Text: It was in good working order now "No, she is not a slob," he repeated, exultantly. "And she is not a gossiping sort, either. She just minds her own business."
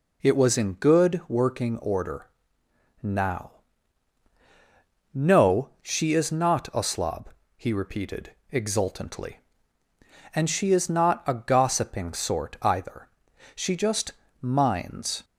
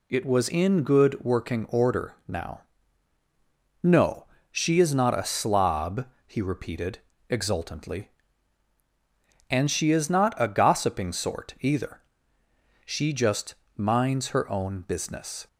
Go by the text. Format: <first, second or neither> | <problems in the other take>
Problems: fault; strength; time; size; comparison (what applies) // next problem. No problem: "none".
second | pauses between "order" and "now"; noticeable; at 2.2 s; 0.76 s long // pauses between "now" and "No"; strong; at 3.5 s; 1.6 s long; also in the second // pauses between "just" and "minds"; slight; at 14.1 s; 0.26 s long; slight in the second // stops before "her own business"; at 15.2 s